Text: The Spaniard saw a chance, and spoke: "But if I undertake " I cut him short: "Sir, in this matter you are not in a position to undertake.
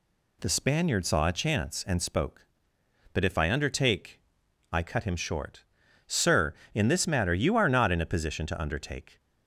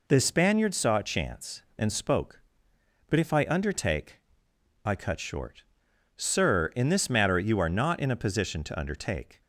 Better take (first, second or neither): first